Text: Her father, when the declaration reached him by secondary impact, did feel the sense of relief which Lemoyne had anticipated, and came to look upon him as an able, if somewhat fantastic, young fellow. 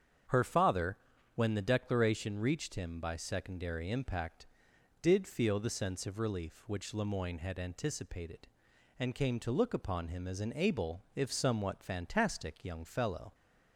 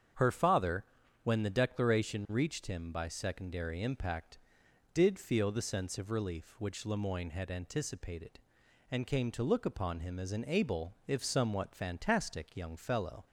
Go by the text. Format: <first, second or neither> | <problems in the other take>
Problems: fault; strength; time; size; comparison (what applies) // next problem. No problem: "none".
neither | starts louder than the rest; strong; the same in both